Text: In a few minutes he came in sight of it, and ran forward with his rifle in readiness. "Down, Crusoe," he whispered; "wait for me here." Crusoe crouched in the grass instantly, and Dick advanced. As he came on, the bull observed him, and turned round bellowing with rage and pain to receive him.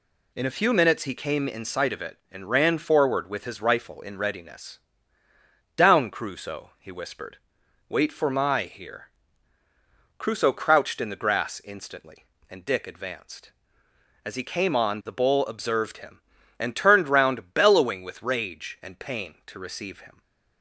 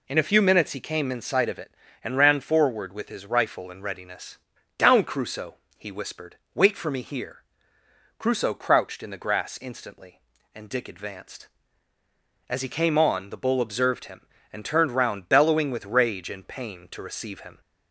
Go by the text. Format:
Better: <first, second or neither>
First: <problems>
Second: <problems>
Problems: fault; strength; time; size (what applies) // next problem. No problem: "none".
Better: second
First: says "my" for "me"; at 8.3 s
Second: none